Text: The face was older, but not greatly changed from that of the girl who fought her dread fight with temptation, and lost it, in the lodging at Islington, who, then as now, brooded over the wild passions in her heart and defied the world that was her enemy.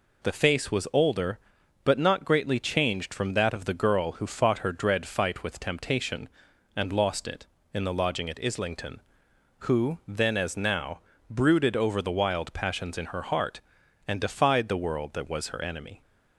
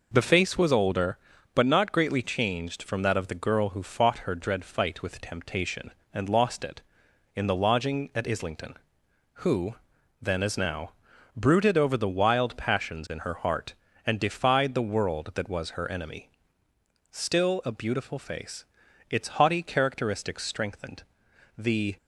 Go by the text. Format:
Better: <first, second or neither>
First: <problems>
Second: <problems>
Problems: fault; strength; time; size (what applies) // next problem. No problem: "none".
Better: first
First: none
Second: goes on to say "Still a beautiful face its haughty characteristics strengthened the"; strong; from 17.1 s on; 4.8 s long